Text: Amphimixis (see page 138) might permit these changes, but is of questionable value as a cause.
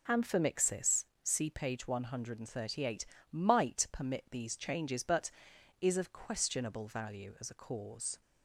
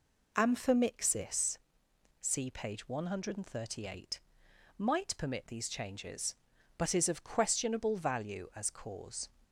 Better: first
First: none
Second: skips "a"; at 8.6 s

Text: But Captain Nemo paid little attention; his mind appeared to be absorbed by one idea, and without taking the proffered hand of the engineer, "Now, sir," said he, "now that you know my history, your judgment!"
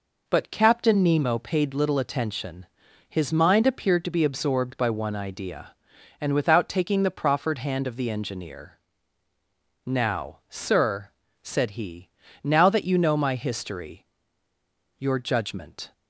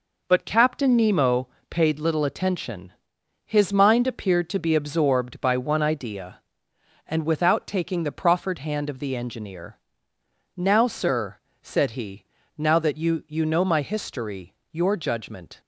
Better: first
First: none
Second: pauses between "Nemo" and "paid"; slight; at 1.4 s; 0.20 s long // says "you" twice; at 13.2 s

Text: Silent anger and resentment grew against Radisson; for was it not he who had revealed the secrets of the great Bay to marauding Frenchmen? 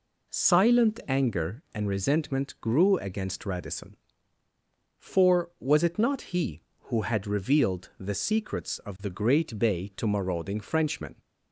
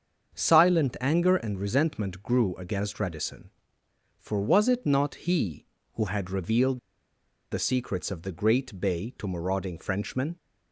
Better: first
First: none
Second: starts louder than the rest; until 1.3 s; 7 dB // pauses between "revealed" and "the"; noticeable; at 6.7 s; 0.72 s long

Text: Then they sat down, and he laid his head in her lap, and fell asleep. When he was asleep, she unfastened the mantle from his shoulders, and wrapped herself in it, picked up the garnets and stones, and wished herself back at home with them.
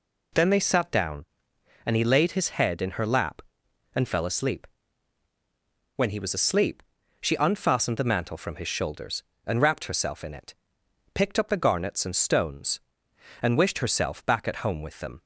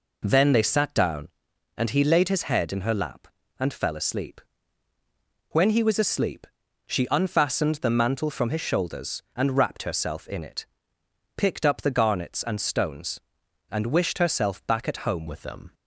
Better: first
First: none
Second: changes voice at "with"; from 15.2 s on; 0.5 s long

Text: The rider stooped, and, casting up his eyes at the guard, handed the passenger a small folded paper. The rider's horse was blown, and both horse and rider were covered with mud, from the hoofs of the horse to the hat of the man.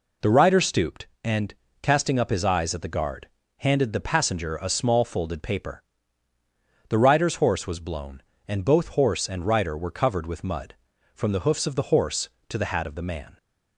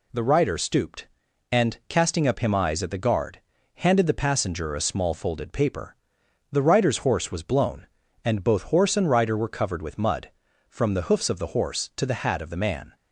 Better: first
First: none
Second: says "him" for "his"; at 2.3 s

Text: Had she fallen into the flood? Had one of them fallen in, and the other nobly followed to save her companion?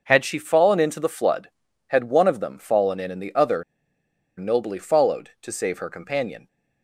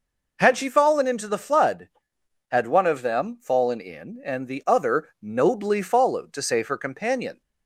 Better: second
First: pauses between "other" and "nobly"; noticeable; at 3.6 s; 0.73 s long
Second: none

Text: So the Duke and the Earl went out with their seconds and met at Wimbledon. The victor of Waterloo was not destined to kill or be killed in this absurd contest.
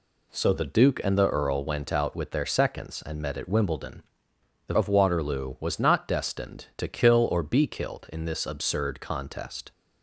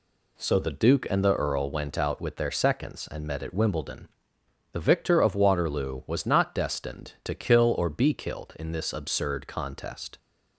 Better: second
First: skips "victor"; at 4.7 s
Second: none

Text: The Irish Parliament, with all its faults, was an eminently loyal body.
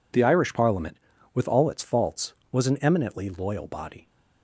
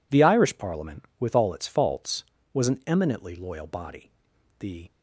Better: first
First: none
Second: goes on to say "The"; slight; from 4.5 s on; 0.32 s long

